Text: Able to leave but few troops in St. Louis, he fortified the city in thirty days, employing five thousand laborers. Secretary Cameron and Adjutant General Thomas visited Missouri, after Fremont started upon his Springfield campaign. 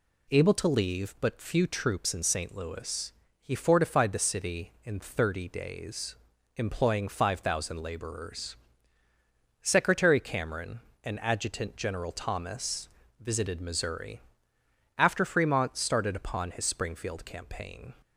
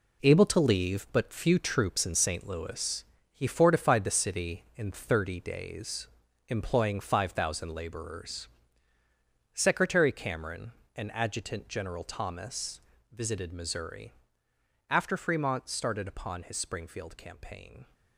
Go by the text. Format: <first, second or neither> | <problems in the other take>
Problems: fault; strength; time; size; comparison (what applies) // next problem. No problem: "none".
first | gets quieter; strong; throughout; 9 dB // pauses between "Thomas" and "visited"; slight; at 12.8 s; 0.30 s long; slight in the first